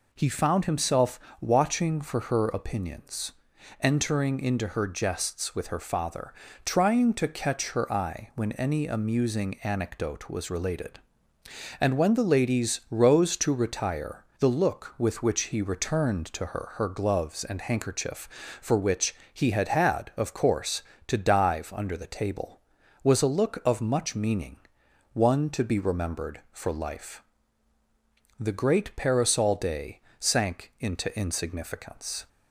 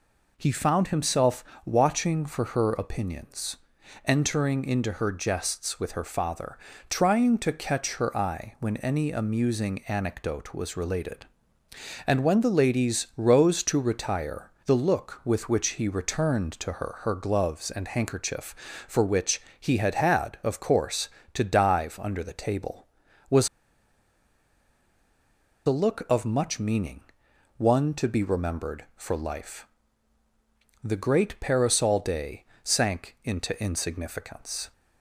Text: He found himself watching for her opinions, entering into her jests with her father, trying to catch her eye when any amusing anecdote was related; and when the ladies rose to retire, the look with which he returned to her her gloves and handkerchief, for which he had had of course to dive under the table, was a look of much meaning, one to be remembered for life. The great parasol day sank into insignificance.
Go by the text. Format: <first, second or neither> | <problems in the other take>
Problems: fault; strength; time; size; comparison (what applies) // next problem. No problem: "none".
first | pauses between "himself" and "watching"; slight; at 1.4 s; 0.20 s long; slight in the first // pauses between "which" and "he"; slight; at 19.4 s; 0.20 s long; slight in the first // pauses between "was" and "a"; strong; at 23.4 s; 2.1 s long // pauses between "day" and "sank"; slight; at 32.4 s; 0.20 s long; slight in the first